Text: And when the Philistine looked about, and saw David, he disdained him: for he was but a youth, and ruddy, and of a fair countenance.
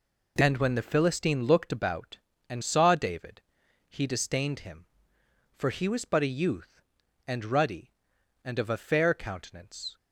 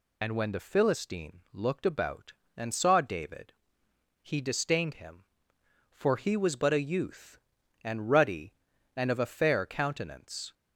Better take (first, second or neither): first